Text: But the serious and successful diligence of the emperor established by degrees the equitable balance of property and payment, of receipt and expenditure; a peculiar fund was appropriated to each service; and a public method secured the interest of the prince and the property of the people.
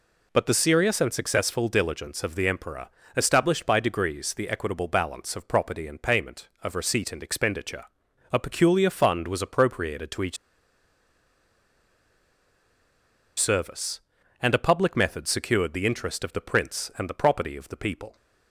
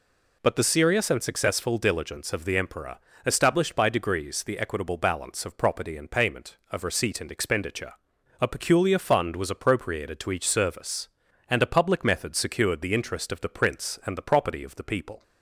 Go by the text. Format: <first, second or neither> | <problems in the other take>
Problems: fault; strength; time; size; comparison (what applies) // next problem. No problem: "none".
second | pauses between "emperor" and "established"; slight; at 2.8 s; 0.28 s long; slight in the second // pauses between "each" and "service"; strong; at 10.3 s; 3.0 s long